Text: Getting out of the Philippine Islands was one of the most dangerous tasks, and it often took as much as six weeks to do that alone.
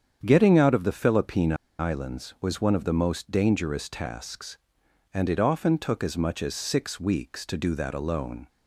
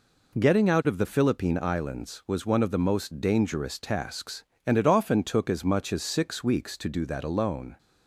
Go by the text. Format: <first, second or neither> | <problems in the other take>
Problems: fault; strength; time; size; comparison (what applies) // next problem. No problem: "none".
second | starts louder than the rest; strong; until 1.2 s; 8 dB // pauses between "Philippine" and "Islands"; slight; at 1.5 s; 0.25 s long